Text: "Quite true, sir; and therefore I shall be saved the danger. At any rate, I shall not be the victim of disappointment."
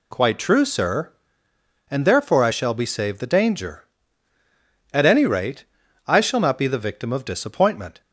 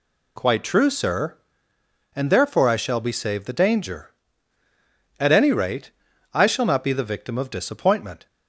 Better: neither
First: none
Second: none

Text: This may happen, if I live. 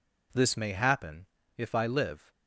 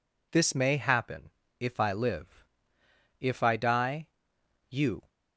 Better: first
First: none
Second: goes on to say "If I die you"; strong; from 3.1 s on; 1.9 s long

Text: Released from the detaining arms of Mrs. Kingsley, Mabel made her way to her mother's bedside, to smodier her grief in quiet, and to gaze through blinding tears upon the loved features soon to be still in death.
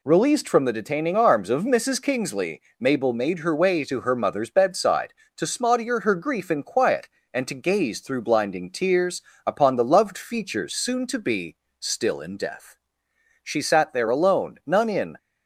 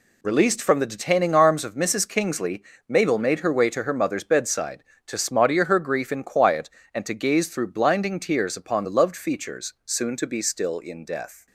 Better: second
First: pauses between "tears" and "upon"; slight; at 9.2 s; 0.24 s long // pauses between "be" and "still"; slight; at 11.5 s; 0.24 s long // goes on to say "She sat there alone none in"; strong; from 13.4 s on; 1.7 s long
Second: none

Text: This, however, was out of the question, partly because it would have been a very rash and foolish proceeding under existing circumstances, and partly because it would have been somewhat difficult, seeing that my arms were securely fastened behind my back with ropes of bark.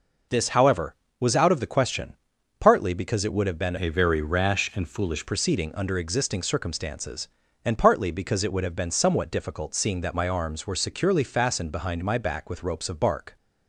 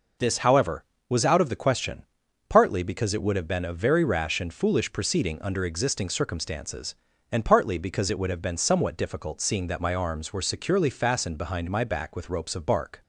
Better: second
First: changes voice from "a" to "foolish"; from 3.7 to 5.2 s; 1.5 s long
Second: none

